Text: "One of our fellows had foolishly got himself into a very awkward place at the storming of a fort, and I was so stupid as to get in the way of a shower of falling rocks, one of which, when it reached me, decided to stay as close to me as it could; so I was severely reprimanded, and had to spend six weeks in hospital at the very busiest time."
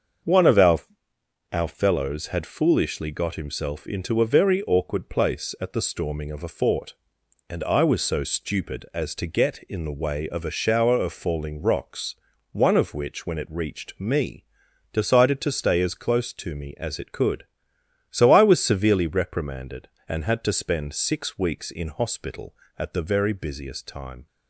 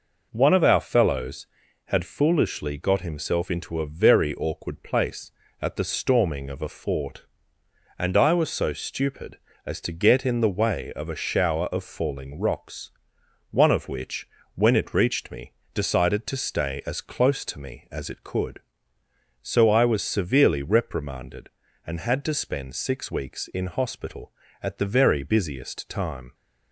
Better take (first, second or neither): second